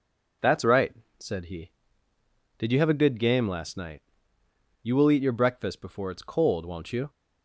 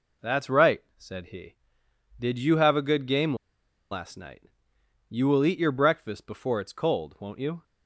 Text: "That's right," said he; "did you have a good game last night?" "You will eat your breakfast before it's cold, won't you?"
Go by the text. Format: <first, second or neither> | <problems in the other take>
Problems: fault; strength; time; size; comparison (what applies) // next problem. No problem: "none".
first | pauses between "game" and "last"; noticeable; at 3.3 s; 0.56 s long